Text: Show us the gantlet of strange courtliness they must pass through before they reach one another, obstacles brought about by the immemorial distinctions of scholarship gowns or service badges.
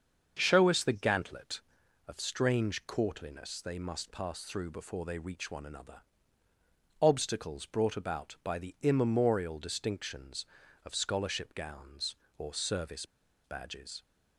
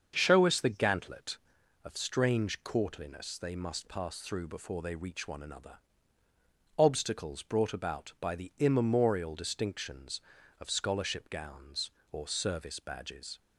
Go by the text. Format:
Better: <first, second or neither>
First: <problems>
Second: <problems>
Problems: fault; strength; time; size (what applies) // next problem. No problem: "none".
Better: second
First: starts louder than the rest; until 1.4 s; 7 dB // pauses between "service" and "badges"; at 13.0 s; 0.40 s long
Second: starts louder than the rest; until 1.1 s; 7 dB